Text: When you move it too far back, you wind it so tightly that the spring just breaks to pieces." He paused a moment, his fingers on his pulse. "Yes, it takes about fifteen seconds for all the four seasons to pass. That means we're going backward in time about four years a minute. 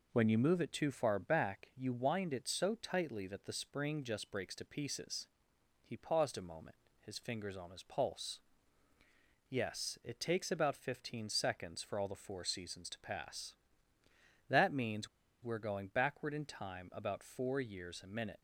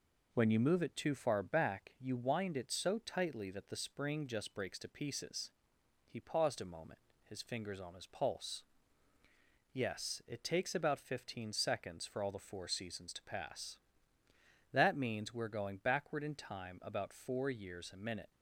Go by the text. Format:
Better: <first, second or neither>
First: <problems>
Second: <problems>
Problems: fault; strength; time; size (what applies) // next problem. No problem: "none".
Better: second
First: pauses between "means" and "we're"; at 15.0 s; 0.36 s long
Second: none